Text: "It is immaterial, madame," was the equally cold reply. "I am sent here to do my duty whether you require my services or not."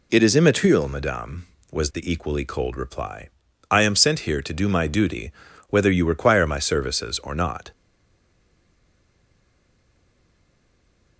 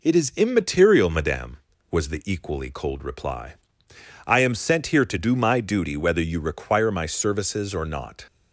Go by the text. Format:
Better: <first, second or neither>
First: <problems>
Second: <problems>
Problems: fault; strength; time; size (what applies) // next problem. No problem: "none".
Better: second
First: pauses between "duty" and "whether"; at 5.3 s; 0.40 s long // stays silent after the last word; strong; from 7.7 s on; 3.4 s long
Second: none